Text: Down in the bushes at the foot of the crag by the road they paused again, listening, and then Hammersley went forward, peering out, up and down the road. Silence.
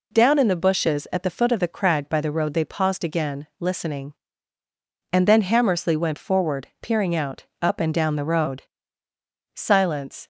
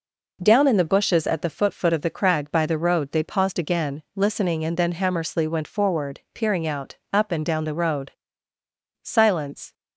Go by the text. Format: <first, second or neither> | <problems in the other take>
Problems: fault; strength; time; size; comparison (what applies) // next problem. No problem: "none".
first | says "foot" twice; at 1.7 s